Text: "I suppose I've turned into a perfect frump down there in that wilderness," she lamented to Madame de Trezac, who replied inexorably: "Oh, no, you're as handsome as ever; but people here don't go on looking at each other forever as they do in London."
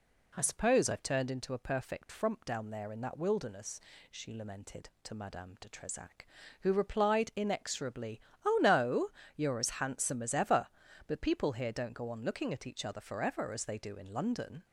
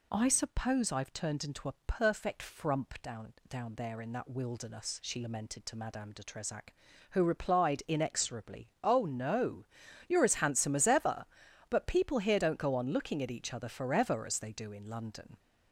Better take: first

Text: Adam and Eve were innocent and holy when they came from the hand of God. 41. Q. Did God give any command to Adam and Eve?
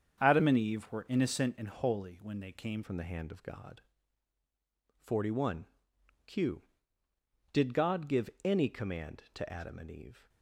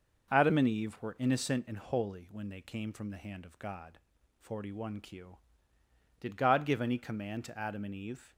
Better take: second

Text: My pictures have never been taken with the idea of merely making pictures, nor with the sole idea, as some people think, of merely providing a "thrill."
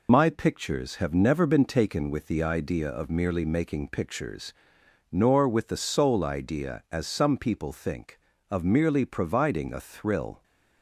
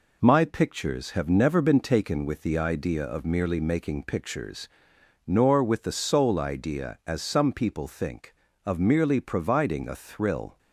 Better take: second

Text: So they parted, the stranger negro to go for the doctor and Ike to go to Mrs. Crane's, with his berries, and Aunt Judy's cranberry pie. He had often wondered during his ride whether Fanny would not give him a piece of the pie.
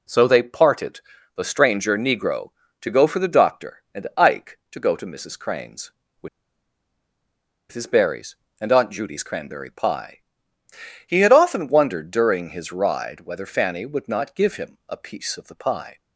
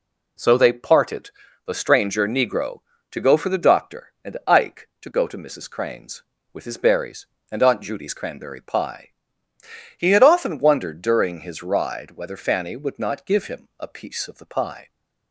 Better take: second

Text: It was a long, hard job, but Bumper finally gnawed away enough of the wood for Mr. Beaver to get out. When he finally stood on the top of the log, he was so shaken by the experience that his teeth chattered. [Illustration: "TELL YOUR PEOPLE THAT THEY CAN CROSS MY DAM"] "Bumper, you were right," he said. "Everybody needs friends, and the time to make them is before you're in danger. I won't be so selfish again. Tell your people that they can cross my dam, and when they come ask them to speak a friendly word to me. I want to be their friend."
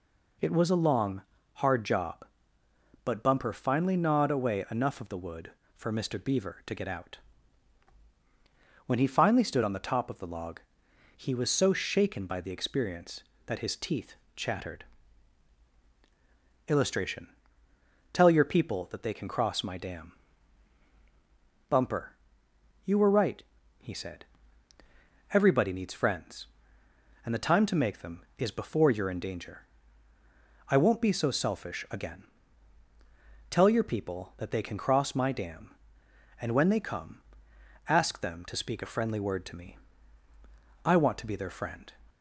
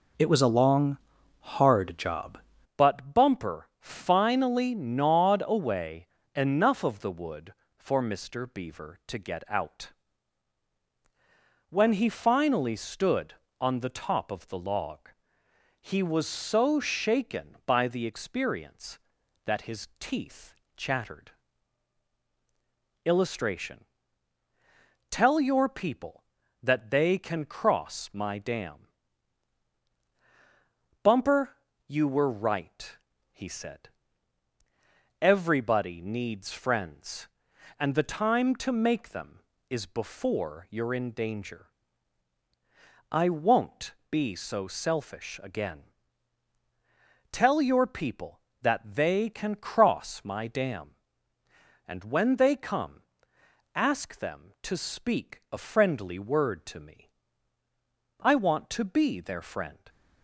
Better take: first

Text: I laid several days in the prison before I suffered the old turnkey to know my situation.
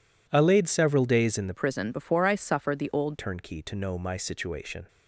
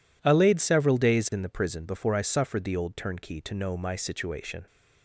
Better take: second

